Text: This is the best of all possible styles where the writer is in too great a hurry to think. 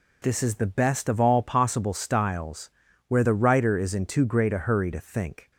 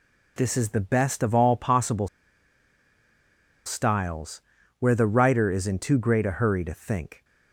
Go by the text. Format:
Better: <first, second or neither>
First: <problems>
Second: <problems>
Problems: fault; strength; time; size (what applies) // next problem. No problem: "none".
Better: first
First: pauses between "styles" and "where"; at 2.6 s; 0.40 s long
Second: pauses between "possible" and "styles"; strong; at 2.0 s; 1.5 s long // pauses between "styles" and "where"; at 4.4 s; 0.40 s long